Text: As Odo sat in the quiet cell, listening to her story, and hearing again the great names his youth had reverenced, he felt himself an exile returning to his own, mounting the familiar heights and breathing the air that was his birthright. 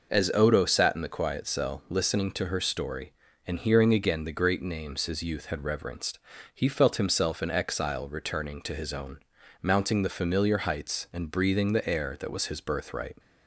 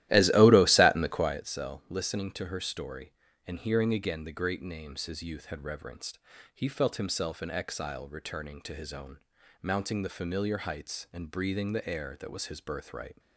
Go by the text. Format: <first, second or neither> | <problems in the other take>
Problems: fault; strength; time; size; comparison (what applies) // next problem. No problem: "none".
first | starts louder than the rest; strong; until 1.5 s; 14.5 dB